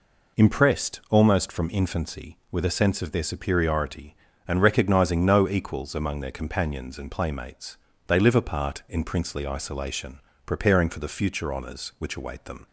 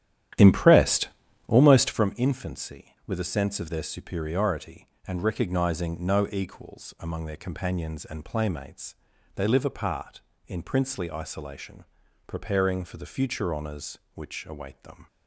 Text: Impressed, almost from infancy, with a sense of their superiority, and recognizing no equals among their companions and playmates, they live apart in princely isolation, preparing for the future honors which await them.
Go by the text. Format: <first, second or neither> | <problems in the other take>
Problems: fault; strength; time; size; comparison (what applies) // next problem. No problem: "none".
first | starts louder than the rest; strong; until 2.1 s; 11 dB